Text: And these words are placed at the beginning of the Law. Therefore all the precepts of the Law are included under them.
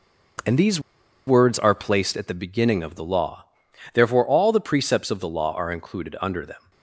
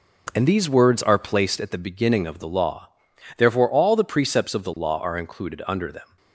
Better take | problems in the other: second | pauses between "these" and "words"; noticeable; at 0.8 s; 0.46 s long

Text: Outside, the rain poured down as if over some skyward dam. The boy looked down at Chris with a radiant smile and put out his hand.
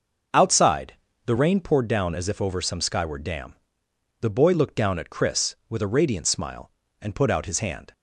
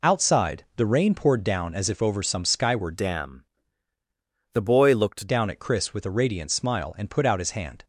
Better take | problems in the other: first | changes voice from "dam" to "looked"; from 2.9 to 5.2 s; 2.3 s long

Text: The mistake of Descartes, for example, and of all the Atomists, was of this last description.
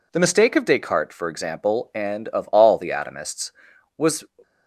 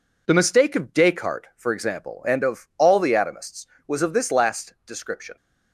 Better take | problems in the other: second | stops before "of this last description"; at 4.4 s

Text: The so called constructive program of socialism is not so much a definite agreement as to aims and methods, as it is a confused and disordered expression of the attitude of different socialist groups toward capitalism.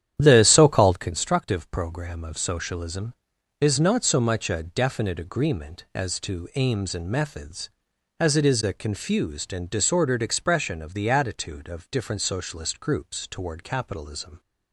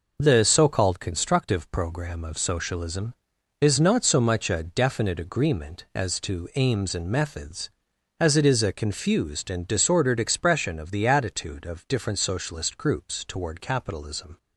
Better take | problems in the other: second | starts louder than the rest; strong; until 1.1 s; 10 dB

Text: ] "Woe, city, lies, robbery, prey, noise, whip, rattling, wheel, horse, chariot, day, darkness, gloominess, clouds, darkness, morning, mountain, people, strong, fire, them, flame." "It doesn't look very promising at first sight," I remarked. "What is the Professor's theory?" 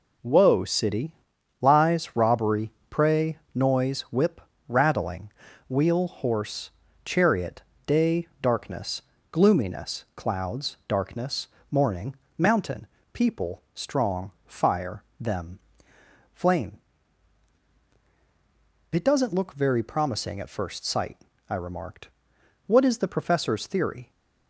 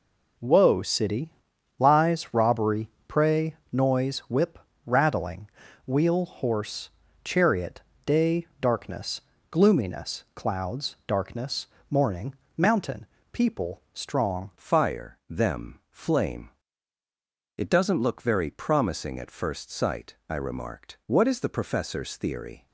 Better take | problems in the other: first | changes voice at "fire"; from 14.5 s on; 8.1 s long

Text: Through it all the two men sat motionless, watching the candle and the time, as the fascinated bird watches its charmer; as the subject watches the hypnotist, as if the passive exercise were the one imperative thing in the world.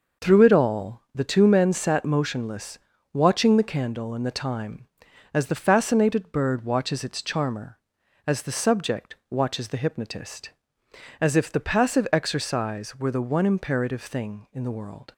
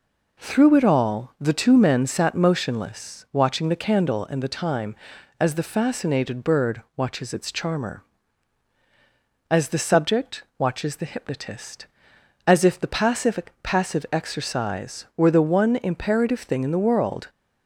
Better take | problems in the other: first | pauses between "subject" and "watches"; slight; at 10.4 s; 0.16 s long // says "passive" twice; at 13.6 s

